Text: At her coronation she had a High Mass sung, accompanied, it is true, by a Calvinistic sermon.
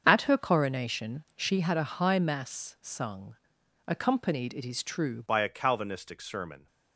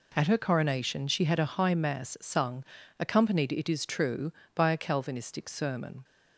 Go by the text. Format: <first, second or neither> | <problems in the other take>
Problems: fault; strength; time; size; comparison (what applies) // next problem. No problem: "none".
second | starts louder than the rest; until 1.0 s; 7 dB // changes voice at "by"; from 5.2 s on; 1.4 s long